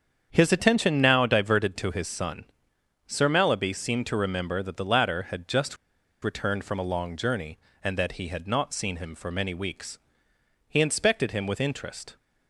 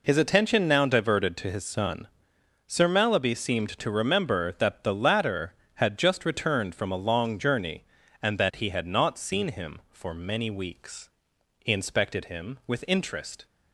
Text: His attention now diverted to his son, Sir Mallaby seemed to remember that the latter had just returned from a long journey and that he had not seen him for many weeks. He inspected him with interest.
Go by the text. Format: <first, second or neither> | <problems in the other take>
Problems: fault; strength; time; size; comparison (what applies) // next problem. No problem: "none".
second | starts louder than the rest; strong; until 1.3 s; 7.5 dB // pauses between "just" and "returned"; at 5.7 s; 0.45 s long